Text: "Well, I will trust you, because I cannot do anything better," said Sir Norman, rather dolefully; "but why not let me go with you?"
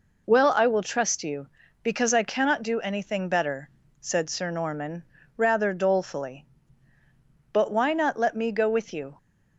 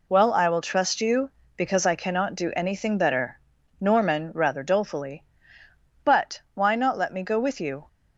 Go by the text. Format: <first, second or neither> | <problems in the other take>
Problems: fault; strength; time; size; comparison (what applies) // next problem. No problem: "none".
first | skips "said Sir"; at 3.5 s